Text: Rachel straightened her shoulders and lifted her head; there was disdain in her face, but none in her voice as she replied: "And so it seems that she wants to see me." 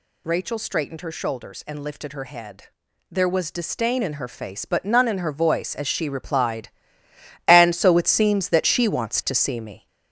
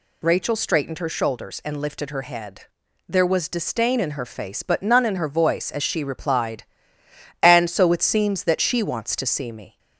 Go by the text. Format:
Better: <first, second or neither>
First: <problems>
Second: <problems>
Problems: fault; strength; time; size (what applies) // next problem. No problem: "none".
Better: second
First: gets louder; noticeable; throughout; 6 dB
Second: none